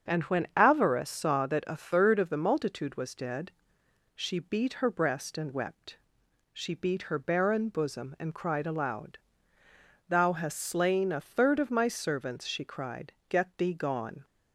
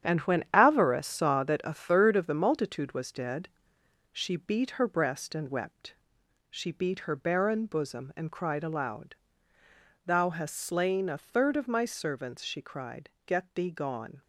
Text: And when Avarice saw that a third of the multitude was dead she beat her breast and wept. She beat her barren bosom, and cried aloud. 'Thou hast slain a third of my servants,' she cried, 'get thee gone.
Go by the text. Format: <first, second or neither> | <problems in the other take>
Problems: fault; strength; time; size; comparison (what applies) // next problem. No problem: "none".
first | gets quieter; strong; throughout; 8.5 dB // starts louder than the rest; strong; until 1.1 s; 9 dB; strong in the first // pauses between "dead" and "she"; noticeable; at 3.4 s; 0.64 s long; noticeable in the first